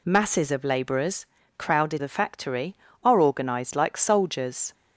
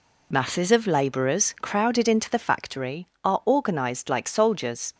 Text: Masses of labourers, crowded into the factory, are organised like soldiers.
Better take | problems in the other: second | skips "into"; at 1.9 s

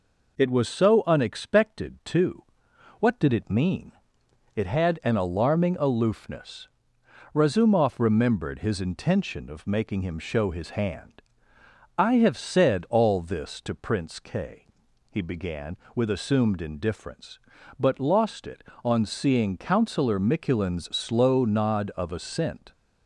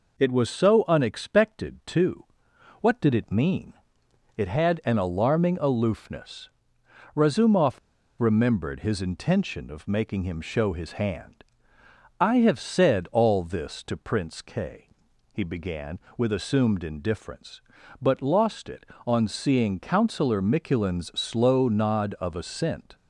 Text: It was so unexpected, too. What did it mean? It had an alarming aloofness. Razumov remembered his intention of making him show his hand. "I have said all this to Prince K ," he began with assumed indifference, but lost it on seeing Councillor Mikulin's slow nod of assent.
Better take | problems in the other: first | pauses between "Razumov" and "remembered"; at 7.7 s; 0.40 s long

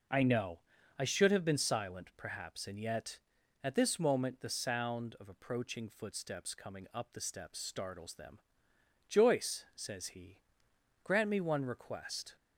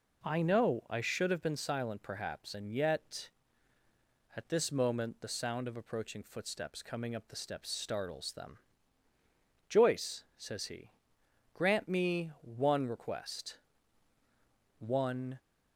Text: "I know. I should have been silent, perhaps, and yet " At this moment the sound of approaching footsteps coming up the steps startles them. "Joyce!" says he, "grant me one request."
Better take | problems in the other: first | goes on to say "One"; from 14.7 s on; 0.60 s long

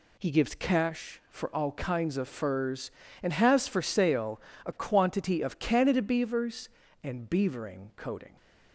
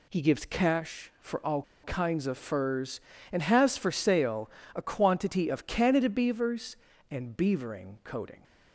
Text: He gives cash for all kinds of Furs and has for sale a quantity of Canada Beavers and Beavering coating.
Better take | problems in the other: first | pauses between "all" and "kinds"; slight; at 1.6 s; 0.21 s long // pauses between "sale" and "a"; slight; at 4.4 s; 0.26 s long; slight in the first

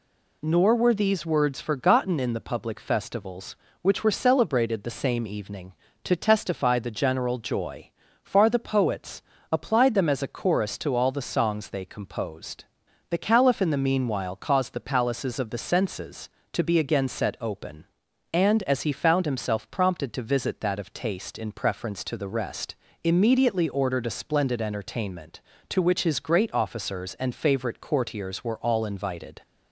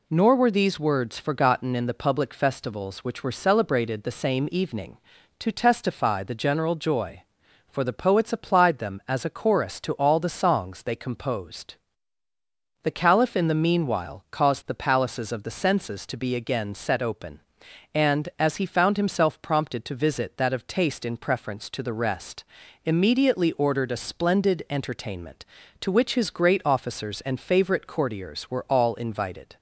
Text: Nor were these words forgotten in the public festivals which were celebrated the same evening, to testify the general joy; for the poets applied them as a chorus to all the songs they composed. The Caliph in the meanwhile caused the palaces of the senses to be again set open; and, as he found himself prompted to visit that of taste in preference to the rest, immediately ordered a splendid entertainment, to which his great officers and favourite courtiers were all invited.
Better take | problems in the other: second | says "far" for "for"; at 8.2 s // pauses between "poets" and "applied"; slight; at 9.1 s; 0.30 s long

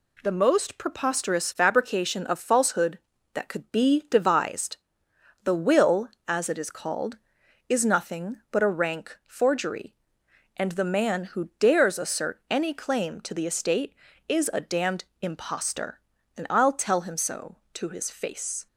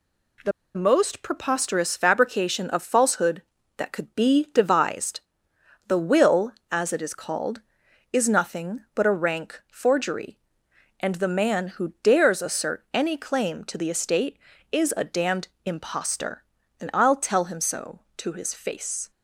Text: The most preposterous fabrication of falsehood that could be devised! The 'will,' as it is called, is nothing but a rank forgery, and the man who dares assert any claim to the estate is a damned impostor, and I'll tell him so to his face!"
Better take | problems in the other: first | pauses between "The" and "most"; slight; at 0.5 s; 0.25 s long // pauses between "damned" and "impostor"; slight; at 15.4 s; 0.16 s long; slight in the first

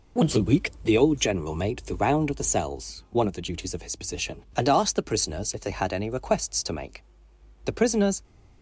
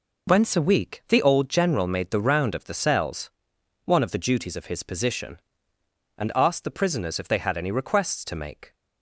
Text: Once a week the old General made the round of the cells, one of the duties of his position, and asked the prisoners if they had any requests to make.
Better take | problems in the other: second | goes on to say "The prisoners"; from 7.6 s on; 0.58 s long

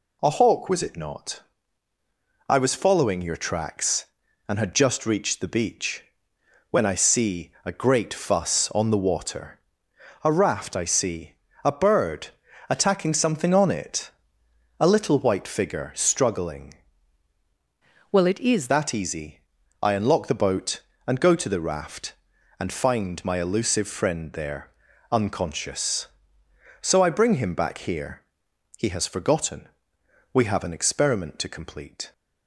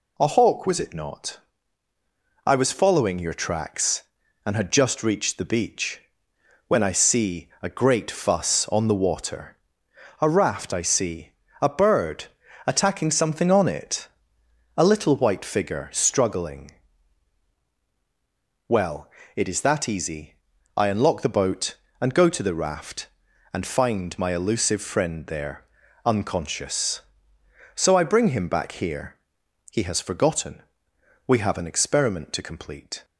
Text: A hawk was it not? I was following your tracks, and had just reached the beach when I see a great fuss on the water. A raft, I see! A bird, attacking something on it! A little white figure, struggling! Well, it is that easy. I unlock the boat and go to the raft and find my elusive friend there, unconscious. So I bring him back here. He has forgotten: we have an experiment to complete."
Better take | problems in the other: second | pauses between "beach" and "when"; noticeable; at 6.0 s; 0.68 s long; noticeable in the second // changes voice from "Well" to "is"; from 18.1 to 18.6 s; 0.5 s long

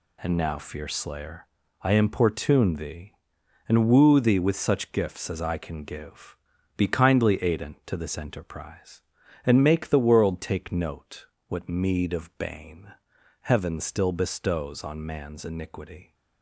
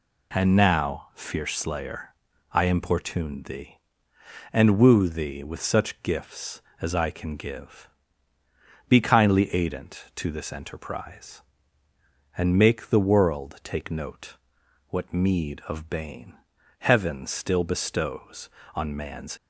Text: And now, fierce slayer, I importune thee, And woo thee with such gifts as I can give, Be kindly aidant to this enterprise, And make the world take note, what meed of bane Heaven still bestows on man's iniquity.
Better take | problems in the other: first | pauses between "bane" and "Heaven"; noticeable; at 16.3 s; 0.46 s long; noticeable in the first // stops before "iniquity"; at 19.3 s

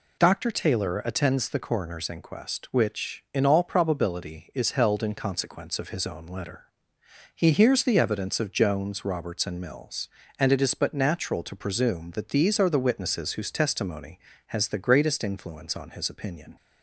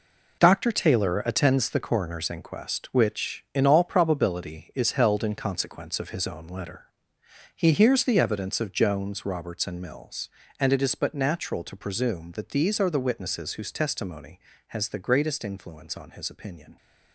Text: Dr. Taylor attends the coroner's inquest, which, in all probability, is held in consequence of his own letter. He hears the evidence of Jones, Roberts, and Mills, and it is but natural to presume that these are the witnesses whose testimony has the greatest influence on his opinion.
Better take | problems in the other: first | gets quieter; strong; throughout; 9.5 dB

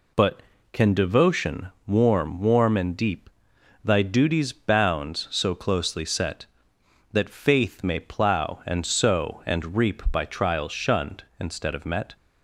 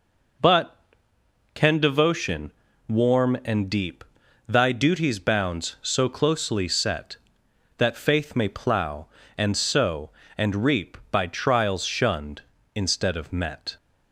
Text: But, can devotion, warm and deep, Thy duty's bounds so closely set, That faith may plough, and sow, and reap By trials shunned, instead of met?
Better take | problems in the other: second | says "warm" twice; at 2.3 s

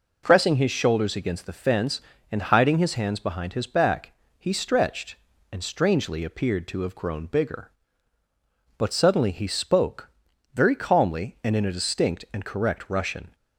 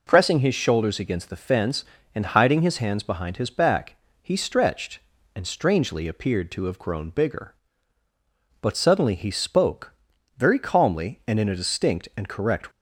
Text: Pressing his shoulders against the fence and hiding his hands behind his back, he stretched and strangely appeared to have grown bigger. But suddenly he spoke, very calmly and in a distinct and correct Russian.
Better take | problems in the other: first | stops before "Russian"; at 12.7 s

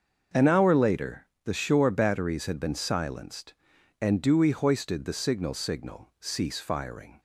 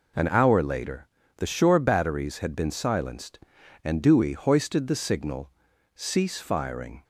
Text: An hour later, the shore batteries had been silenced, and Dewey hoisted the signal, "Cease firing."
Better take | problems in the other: second | starts louder than the rest; until 1.5 s; 6.5 dB // says "signal" twice; at 5.5 s

